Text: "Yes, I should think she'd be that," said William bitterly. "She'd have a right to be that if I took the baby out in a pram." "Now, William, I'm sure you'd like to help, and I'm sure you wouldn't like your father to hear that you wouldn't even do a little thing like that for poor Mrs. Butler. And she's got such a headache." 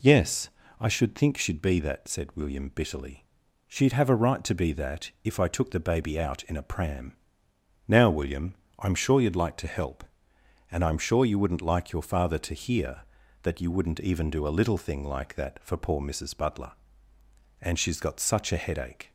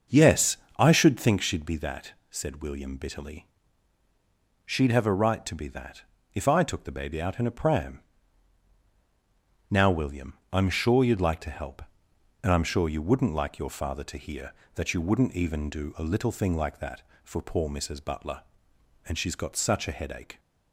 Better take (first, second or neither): first